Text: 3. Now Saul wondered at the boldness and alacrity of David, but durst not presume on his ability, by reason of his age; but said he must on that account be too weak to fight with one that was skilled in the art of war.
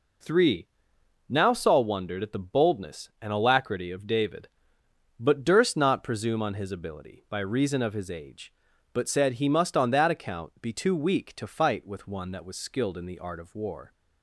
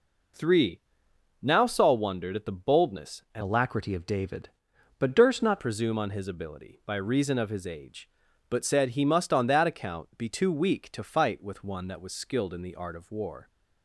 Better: first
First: none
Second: changes voice from "alacrity" to "not"; from 3.4 to 5.6 s; 2.2 s long

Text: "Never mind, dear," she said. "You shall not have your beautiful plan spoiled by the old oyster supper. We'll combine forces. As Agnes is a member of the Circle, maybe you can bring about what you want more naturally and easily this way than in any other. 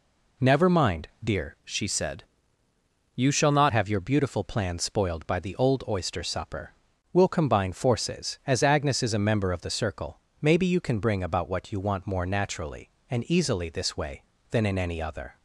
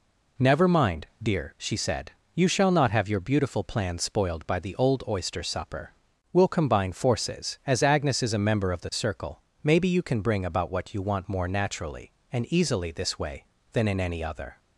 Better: second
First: changes voice from "she" to "not"; from 1.6 to 3.7 s; 2.1 s long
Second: none

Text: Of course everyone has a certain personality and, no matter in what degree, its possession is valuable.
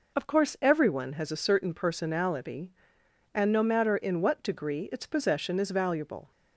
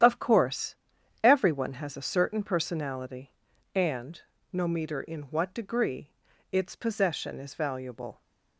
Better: first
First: none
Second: starts louder than the rest; strong; until 1.5 s; 10.5 dB // pauses between "course" and "everyone"; noticeable; at 0.7 s; 0.48 s long // says "meter" for "matter"; at 4.6 s

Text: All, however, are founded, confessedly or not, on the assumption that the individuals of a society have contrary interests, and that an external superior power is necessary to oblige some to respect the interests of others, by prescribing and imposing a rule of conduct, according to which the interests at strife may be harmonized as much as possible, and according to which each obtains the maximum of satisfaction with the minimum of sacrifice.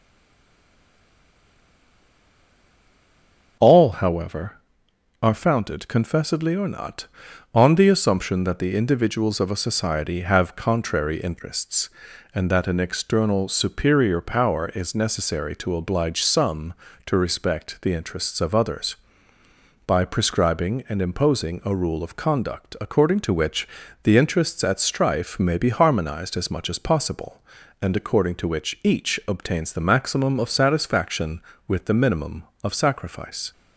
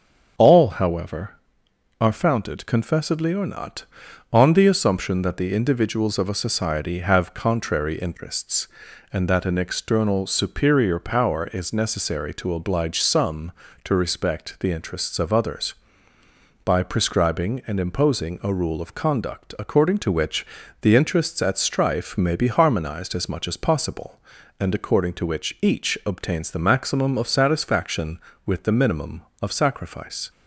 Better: second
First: stays silent before the first word; strong; until 3.5 s; 3.5 s long // starts louder than the rest; until 5.2 s; 7 dB // pauses between "which" and "the"; at 23.6 s; 0.38 s long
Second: starts louder than the rest; until 1.9 s; 7 dB // pauses between "which" and "the"; at 20.4 s; 0.38 s long

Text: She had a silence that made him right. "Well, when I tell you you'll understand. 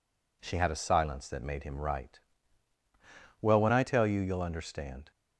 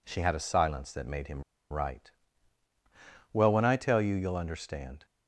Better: first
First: none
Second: pauses between "him" and "right"; slight; at 1.4 s; 0.28 s long

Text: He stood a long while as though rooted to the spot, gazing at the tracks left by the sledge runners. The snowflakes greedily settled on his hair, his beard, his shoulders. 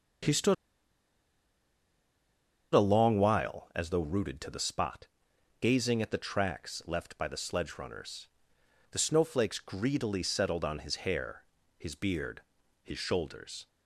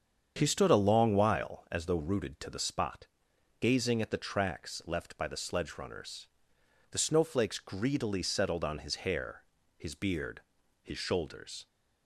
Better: second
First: starts louder than the rest; strong; until 3.4 s; 7.5 dB // pauses between "stood" and "a"; strong; at 0.5 s; 2.1 s long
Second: starts louder than the rest; strong; until 1.3 s; 7.5 dB

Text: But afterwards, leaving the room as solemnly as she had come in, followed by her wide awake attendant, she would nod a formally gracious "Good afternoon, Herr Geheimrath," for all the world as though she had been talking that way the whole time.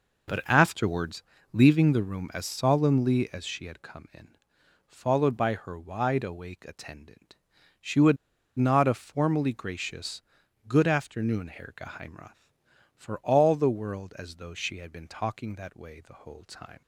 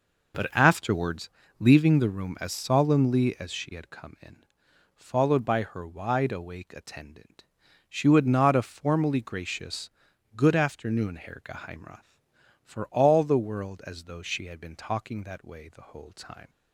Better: second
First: pauses between "would" and "nod"; at 8.1 s; 0.42 s long // pauses between "gracious" and "Good"; noticeable; at 10.2 s; 0.46 s long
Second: pauses between "gracious" and "Good"; noticeable; at 9.8 s; 0.46 s long

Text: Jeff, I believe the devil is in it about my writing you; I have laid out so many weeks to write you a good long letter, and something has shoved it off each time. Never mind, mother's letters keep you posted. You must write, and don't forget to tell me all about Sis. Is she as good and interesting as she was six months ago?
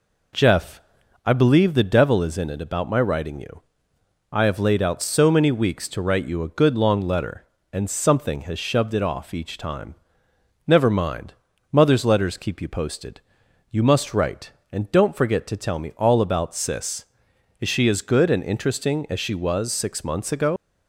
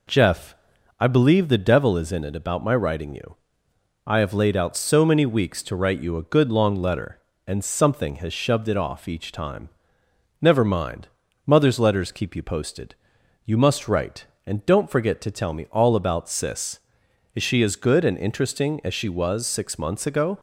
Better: second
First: leaves "ago" unfinished; at 20.5 s; 90 ms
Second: none

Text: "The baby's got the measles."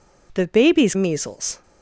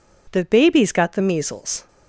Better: second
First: skips "got the"; at 0.9 s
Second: none

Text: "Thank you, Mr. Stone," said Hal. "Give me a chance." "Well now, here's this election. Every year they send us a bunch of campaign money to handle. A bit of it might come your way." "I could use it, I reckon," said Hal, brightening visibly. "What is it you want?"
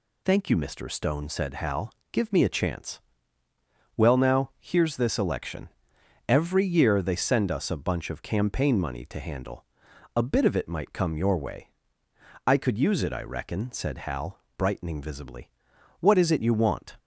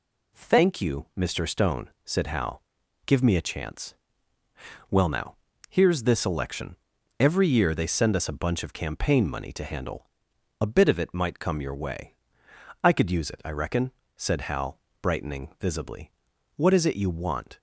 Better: neither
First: none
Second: none

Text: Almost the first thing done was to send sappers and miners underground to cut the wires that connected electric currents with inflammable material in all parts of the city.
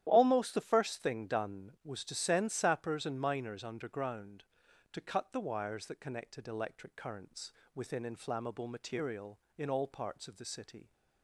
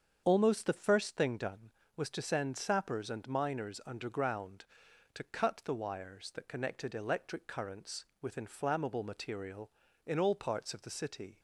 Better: second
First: starts louder than the rest; strong; until 1.0 s; 11.5 dB // says "within" for "with"; at 7.7 s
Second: starts louder than the rest; strong; until 1.2 s; 7.5 dB

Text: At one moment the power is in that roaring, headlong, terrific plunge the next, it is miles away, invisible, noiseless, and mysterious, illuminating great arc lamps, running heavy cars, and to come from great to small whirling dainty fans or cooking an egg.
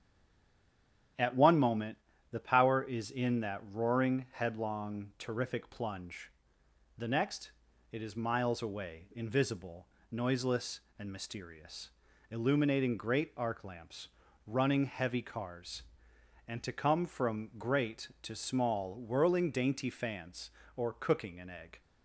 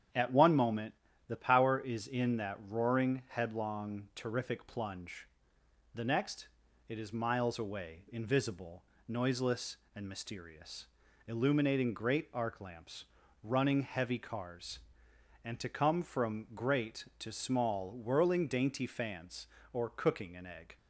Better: second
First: stays silent before the first word; until 1.1 s; 1.1 s long // starts louder than the rest; strong; until 2.5 s; 8.5 dB // pauses between "moment" and "the"; slight; at 1.9 s; 0.36 s long // pauses between "plunge" and "the"; noticeable; at 6.3 s; 0.66 s long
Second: starts louder than the rest; strong; until 1.5 s; 9 dB // pauses between "moment" and "the"; slight; at 0.9 s; 0.36 s long // pauses between "plunge" and "the"; noticeable; at 5.2 s; 0.66 s long

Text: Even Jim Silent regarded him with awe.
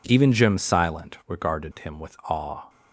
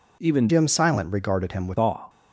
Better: first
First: none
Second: changes voice from "Jim" to "with"; from 0.4 to 1.7 s; 1.3 s long

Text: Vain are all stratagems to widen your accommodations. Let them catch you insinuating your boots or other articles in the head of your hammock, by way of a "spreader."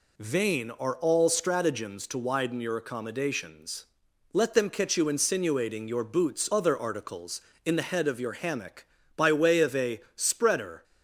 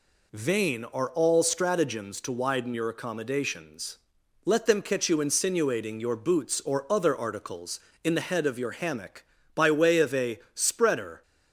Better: second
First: skips "or"; at 6.4 s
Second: none

